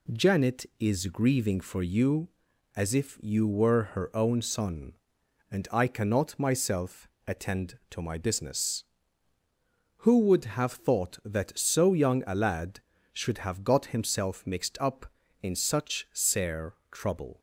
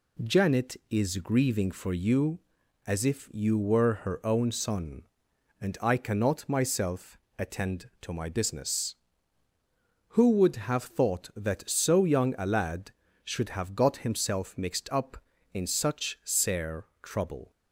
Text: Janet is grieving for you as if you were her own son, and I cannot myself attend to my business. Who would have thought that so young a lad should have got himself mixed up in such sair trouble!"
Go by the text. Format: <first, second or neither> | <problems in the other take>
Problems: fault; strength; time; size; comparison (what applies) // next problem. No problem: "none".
neither | pauses between "myself" and "attend"; slight; the same in both // pauses between "sair" and "trouble"; slight; the same in both